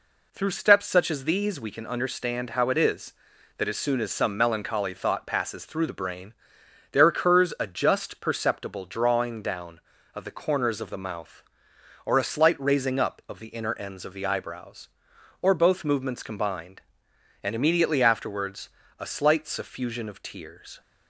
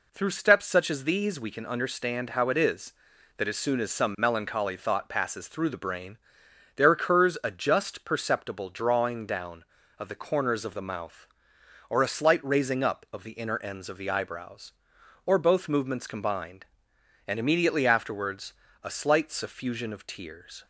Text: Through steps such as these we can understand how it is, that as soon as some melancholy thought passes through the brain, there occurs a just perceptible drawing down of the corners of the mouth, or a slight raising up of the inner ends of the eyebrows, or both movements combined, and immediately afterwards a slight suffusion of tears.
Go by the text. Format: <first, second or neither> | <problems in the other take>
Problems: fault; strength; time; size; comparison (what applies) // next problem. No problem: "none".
neither | pauses between "afterwards" and "a"; slight; the same in both